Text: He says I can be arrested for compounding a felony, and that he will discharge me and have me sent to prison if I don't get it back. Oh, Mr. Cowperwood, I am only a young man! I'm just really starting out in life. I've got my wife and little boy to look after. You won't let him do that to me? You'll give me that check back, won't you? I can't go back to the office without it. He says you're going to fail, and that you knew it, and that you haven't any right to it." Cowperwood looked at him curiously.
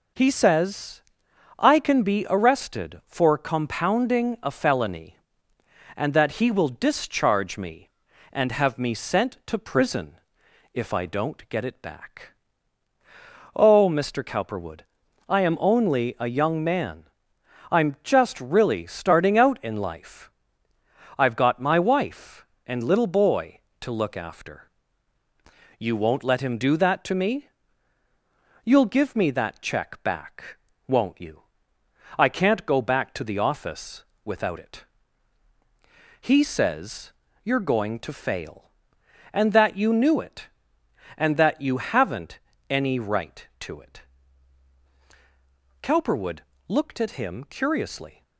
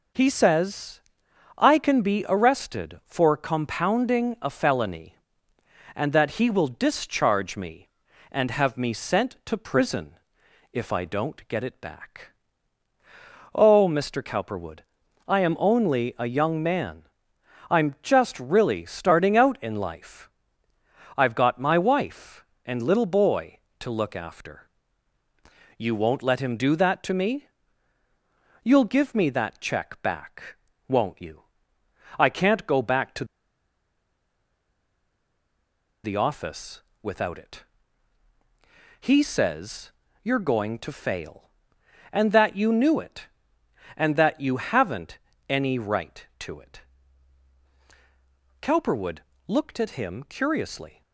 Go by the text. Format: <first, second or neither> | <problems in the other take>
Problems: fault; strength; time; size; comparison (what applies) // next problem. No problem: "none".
first | pauses between "says" and "I"; noticeable; at 1.0 s; 0.56 s long; noticeable in the first // pauses between "prison" and "if"; noticeable; at 10.1 s; 0.58 s long; noticeable in the first // pauses between "to" and "the"; strong; at 33.2 s; 2.7 s long // pauses between "office" and "without"; slight; at 36.8 s; 0.20 s long; slight in the first // pauses between "says" and "you're"; slight; at 39.9 s; 0.32 s long; slight in the first // pauses between "haven't" and "any"; slight; at 45.1 s; 0.30 s long; slight in the first // pauses between "Cowperwood" and "looked"; slight; at 49.1 s; 0.26 s long; slight in the first